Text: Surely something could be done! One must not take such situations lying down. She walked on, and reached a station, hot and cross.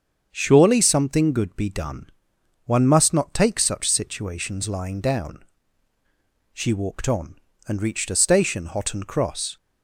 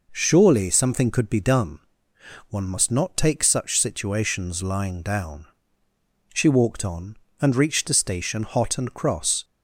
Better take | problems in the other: second | starts louder than the rest; until 1.3 s; 7 dB // says "good" for "could"; at 1.3 s

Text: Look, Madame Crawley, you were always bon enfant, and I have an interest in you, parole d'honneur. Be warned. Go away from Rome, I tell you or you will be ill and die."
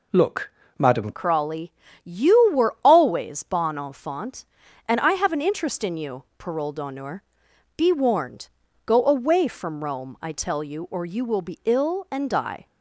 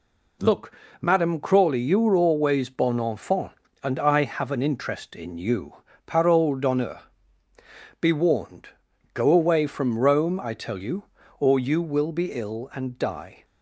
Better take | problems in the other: second | changes voice at "Crawley"; from 1.1 s on; 11.5 s long

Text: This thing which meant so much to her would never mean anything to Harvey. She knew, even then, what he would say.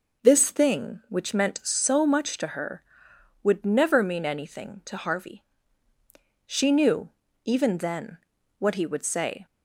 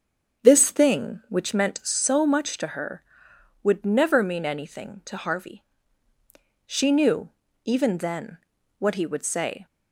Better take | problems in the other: first | starts louder than the rest; until 1.6 s; 7 dB

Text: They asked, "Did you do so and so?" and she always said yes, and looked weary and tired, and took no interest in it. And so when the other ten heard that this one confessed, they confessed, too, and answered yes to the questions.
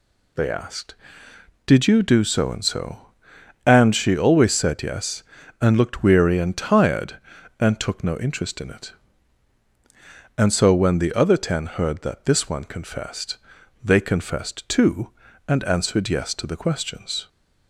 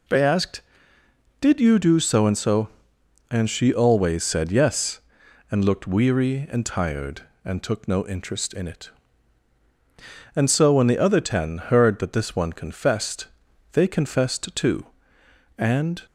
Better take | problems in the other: first | stops before "answered yes to the questions"; at 16.0 s

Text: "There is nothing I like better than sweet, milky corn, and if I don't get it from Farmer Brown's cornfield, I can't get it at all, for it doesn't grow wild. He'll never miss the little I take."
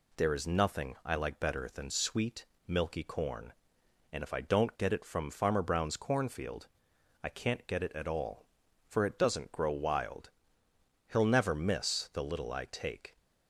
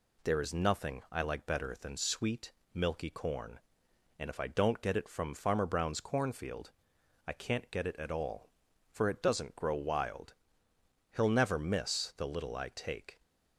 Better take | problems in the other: neither | none

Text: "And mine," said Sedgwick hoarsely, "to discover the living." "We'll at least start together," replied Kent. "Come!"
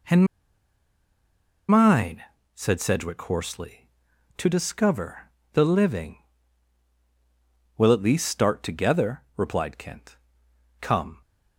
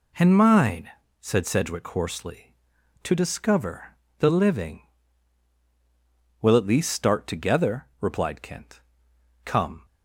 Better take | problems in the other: second | pauses between "And" and "mine"; strong; at 0.2 s; 1.4 s long // pauses between "discover" and "the"; slight; at 5.2 s; 0.24 s long; slight in the second

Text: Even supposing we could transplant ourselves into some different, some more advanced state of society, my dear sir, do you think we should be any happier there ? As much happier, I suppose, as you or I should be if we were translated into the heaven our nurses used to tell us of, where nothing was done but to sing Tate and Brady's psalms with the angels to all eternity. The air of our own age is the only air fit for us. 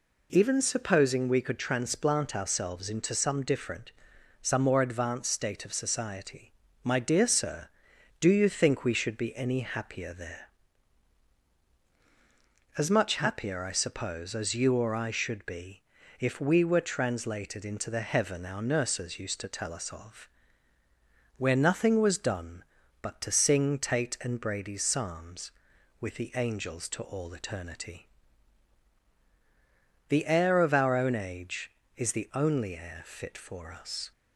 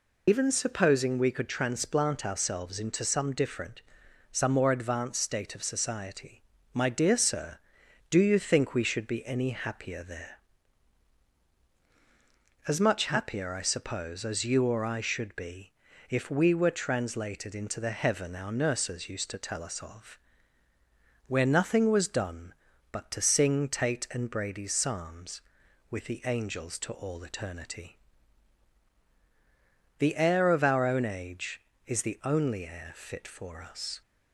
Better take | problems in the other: first | loses the start of "Even"; at 0.2 s; 75 ms // pauses between "be" and "if"; at 15.7 s; 0.40 s long; also in the first

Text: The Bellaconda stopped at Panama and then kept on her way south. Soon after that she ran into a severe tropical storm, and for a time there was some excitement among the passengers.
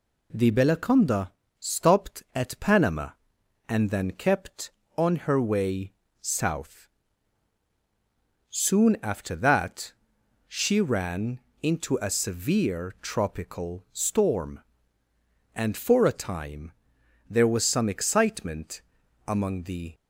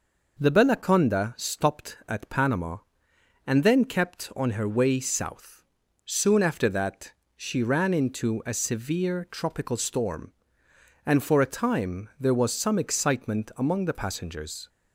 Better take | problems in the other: second | pauses between "Bellaconda" and "stopped"; slight; at 1.3 s; 0.28 s long // pauses between "way" and "south"; slight; at 5.9 s; 0.30 s long // pauses between "that" and "she"; noticeable; at 9.9 s; 0.56 s long; slight in the second // pauses between "ran" and "into"; slight; at 11.3 s; 0.23 s long // pauses between "time" and "there"; noticeable; at 16.7 s; 0.56 s long // pauses between "excitement" and "among"; at 18.8 s; 0.44 s long // stops before "passengers"; at 19.9 s

